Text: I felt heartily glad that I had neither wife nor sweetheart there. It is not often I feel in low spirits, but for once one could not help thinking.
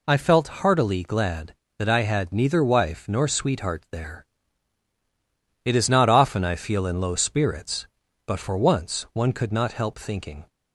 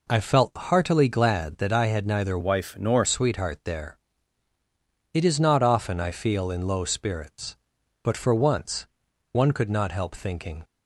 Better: first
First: none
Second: changes voice from "wife" to "nor"; from 2.4 to 3.0 s; 0.6 s long // pauses between "once" and "one"; noticeable; at 8.8 s; 0.48 s long

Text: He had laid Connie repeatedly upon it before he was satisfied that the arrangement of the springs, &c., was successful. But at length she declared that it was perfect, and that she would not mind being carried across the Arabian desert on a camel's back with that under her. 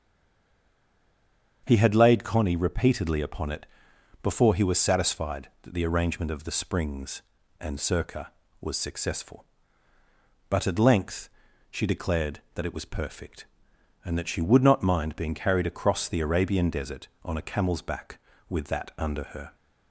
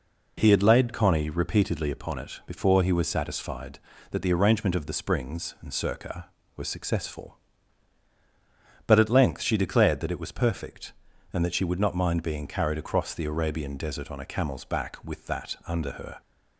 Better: second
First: stays silent before the first word; noticeable; until 1.6 s; 1.6 s long // starts louder than the rest; strong; until 2.6 s; 7.5 dB // pauses between "it" and "before"; noticeable; at 3.6 s; 0.56 s long // pauses between "length" and "she"; at 11.2 s; 0.42 s long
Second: none

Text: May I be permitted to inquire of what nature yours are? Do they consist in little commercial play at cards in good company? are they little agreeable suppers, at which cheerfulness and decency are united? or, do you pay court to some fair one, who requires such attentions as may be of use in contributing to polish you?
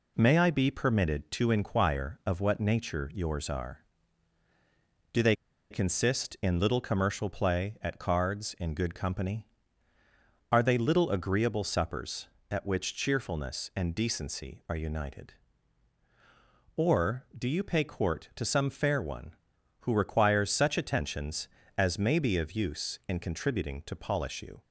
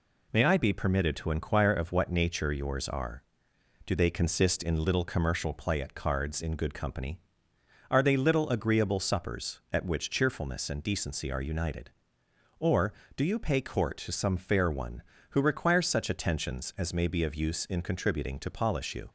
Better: second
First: pauses between "they" and "consist"; at 5.3 s; 0.36 s long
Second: none

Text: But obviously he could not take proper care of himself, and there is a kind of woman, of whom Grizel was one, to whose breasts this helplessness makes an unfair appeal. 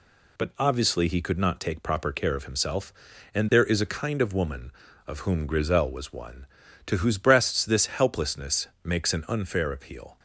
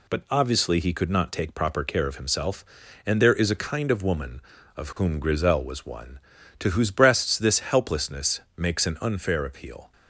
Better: neither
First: pauses between "helplessness" and "makes"; slight; at 8.6 s; 0.16 s long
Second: pauses between "helplessness" and "makes"; slight; at 8.3 s; 0.16 s long

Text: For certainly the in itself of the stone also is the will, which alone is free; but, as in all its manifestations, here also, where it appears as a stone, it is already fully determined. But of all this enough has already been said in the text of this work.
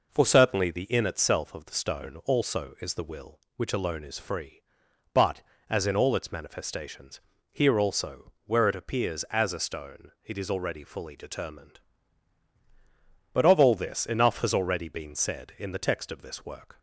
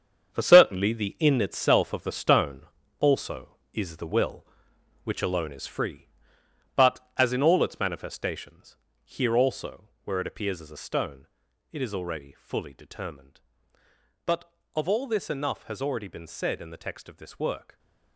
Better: first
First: none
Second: gets quieter; strong; throughout; 11 dB // pauses between "stone" and "also"; at 2.6 s; 0.38 s long

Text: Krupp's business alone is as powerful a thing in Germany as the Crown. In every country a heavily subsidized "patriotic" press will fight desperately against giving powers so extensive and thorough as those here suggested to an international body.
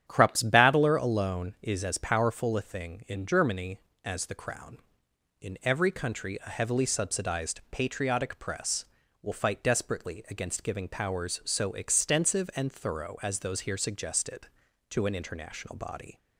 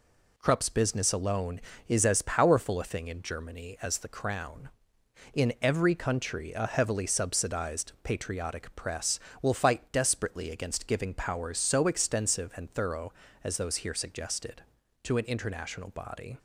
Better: second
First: starts louder than the rest; strong; until 1.0 s; 9.5 dB // says "battler" for "business"; at 0.4 s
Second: none

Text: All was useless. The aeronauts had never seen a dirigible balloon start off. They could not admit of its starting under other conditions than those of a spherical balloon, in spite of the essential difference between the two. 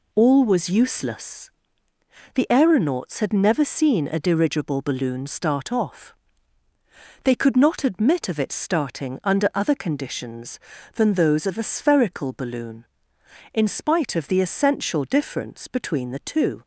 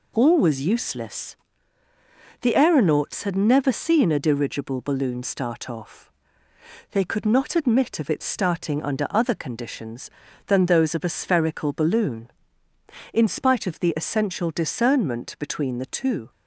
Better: first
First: none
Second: says "discernment" for "difference"; at 14.5 s

